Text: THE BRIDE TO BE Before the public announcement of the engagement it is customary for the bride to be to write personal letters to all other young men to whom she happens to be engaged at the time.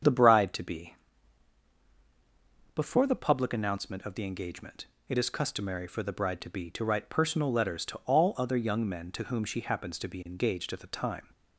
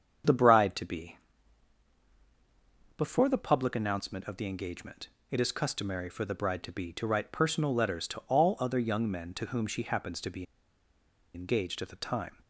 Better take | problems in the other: first | starts louder than the rest; strong; until 3.0 s; 7.5 dB; strong in the first // pauses between "BE" and "Before"; strong; at 1.1 s; 1.8 s long; strong in the first // pauses between "engagement" and "it"; slight; at 5.0 s; 0.22 s long; slight in the first // pauses between "be" and "engaged"; noticeable; at 10.4 s; 0.91 s long

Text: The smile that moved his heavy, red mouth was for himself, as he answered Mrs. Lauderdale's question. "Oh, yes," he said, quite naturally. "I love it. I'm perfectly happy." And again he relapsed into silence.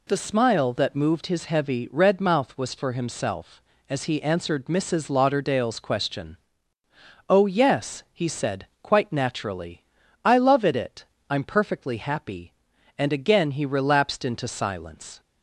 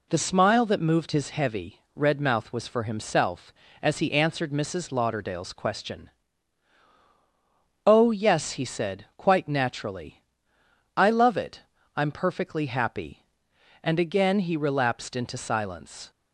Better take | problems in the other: second | says "it" twice; at 10.7 s

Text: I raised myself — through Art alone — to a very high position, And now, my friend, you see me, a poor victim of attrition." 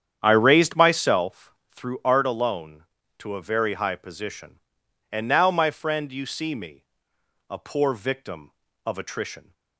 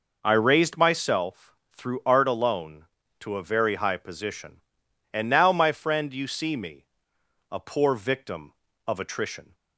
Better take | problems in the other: second | starts louder than the rest; strong; until 1.8 s; 8.5 dB

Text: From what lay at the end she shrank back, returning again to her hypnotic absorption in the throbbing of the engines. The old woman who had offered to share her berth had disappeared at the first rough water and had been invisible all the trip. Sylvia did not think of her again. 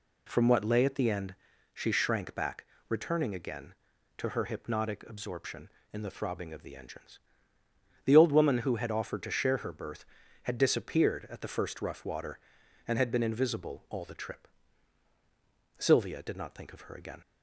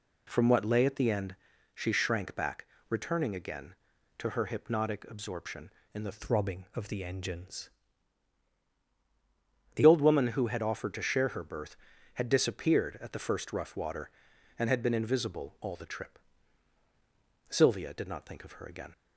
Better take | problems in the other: first | pauses between "end" and "she"; at 1.3 s; 0.38 s long; also in the first // changes voice from "throbbing" to "The"; from 6.1 to 9.8 s; 3.7 s long

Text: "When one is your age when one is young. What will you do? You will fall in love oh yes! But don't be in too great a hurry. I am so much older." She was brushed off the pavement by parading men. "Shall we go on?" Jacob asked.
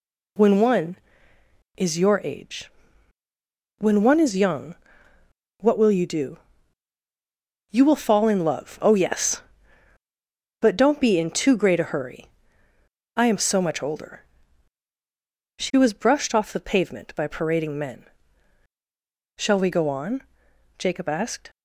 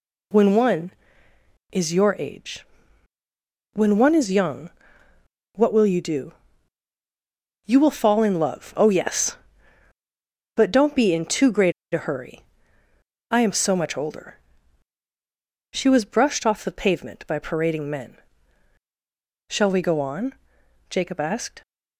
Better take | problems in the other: first | pauses between "age" and "when"; at 2.6 s; 1.1 s long; also in the first // pauses between "great" and "a"; slight; at 11.7 s; 0.21 s long

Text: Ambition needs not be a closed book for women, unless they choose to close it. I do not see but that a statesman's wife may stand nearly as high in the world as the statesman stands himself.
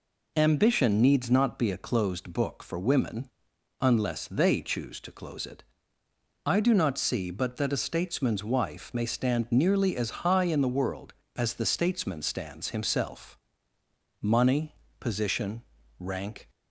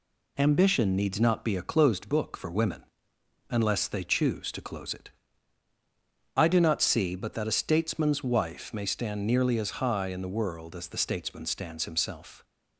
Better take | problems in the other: second | goes on to say "Money position rank"; strong; from 14.2 s on; 2.2 s long

